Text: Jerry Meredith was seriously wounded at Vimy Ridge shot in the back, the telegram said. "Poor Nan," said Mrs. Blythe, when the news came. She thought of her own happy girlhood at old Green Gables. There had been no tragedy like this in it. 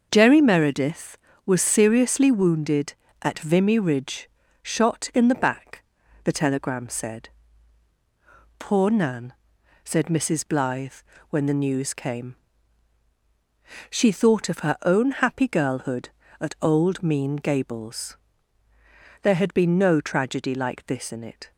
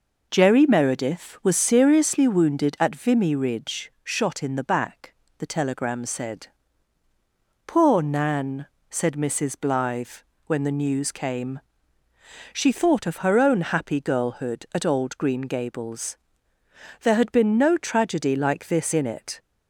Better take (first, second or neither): second